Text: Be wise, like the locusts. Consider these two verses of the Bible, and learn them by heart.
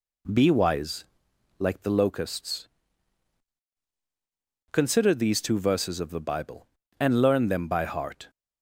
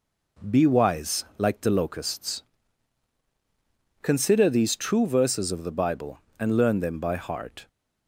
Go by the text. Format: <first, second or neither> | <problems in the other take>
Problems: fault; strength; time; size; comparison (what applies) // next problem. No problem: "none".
first | says "true" for "two"; at 4.7 s